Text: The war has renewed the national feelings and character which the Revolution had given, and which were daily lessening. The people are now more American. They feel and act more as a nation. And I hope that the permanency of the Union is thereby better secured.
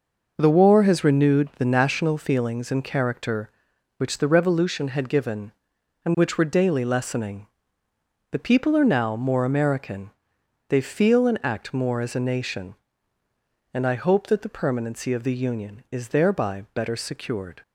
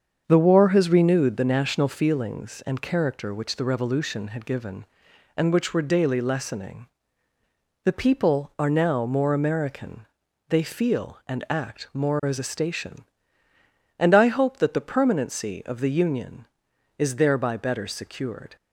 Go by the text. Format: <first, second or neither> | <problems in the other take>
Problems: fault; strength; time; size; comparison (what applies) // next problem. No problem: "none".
first | starts louder than the rest; until 1.2 s; 7 dB // says "station" for "nation"; at 12.4 s